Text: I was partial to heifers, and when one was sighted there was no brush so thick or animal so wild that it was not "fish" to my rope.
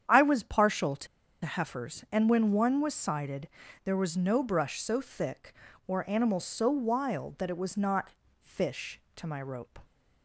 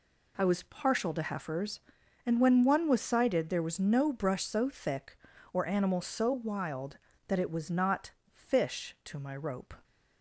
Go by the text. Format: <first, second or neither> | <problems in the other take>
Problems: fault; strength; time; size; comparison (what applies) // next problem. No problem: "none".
second | starts louder than the rest; strong; until 1.4 s; 8.5 dB // pauses between "to" and "heifers"; at 1.0 s; 0.37 s long // pauses between "sighted" and "there"; slight; at 3.4 s; 0.34 s long // pauses between "not" and "fish"; slight; at 8.1 s; 0.30 s long; slight in the second